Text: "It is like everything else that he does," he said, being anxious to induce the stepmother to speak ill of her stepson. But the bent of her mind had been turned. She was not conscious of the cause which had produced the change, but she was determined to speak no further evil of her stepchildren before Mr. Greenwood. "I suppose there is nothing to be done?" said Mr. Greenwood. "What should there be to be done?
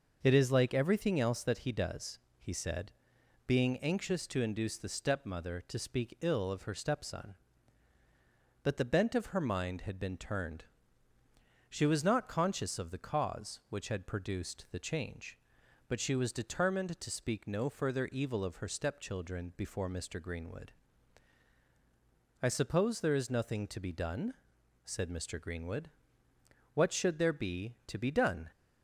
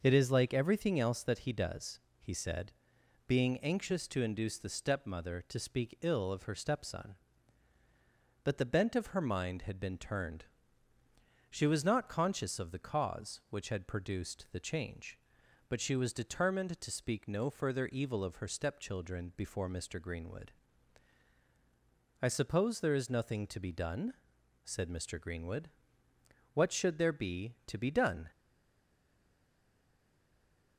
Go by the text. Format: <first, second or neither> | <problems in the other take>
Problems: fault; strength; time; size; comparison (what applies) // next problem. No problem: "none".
first | stays silent after the last word; from 28.3 s on; 2.4 s long